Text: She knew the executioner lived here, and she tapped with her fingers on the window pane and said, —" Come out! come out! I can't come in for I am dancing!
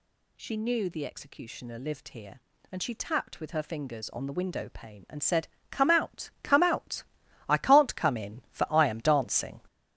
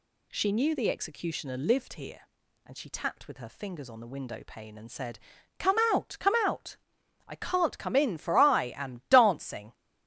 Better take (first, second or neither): second